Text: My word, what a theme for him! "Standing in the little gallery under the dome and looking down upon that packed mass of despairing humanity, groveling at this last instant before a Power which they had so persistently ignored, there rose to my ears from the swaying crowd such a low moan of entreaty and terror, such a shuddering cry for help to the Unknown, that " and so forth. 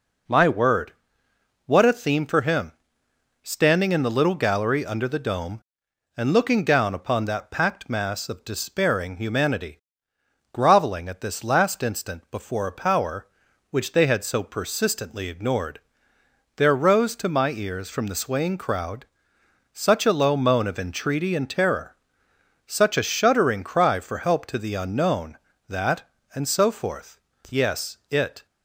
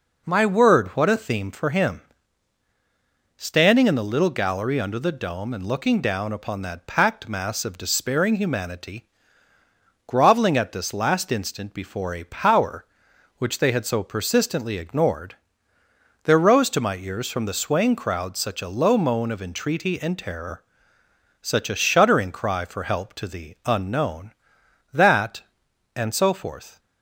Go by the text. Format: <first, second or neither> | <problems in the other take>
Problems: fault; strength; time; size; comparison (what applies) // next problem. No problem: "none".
second | pauses between "crowd" and "such"; noticeable; at 19.0 s; 0.68 s long // goes on to say "Yes it"; noticeable; from 27.5 s on; 0.94 s long